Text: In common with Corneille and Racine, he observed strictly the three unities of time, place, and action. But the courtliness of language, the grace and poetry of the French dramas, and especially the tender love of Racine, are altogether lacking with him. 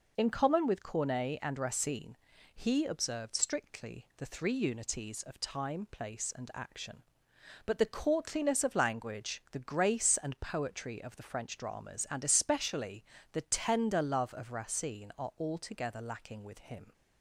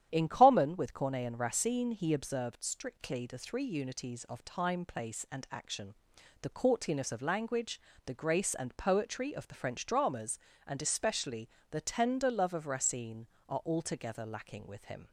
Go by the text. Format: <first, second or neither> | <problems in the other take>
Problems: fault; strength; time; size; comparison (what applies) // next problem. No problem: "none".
first | starts louder than the rest; strong; until 1.1 s; 10 dB // skips "But"; at 6.1 s // pauses between "especially" and "the"; slight; at 11.4 s; 0.20 s long; slight in the first